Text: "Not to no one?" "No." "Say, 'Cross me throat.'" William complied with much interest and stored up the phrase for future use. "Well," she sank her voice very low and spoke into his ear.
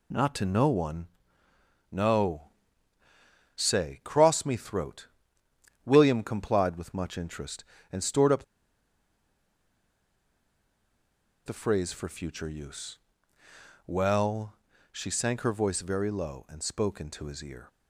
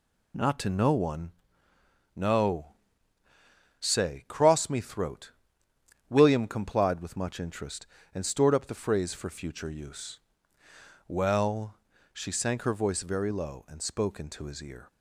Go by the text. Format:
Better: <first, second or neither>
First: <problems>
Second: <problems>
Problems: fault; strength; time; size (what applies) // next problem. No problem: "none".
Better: second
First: pauses between "up" and "the"; strong; at 8.4 s; 3.0 s long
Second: none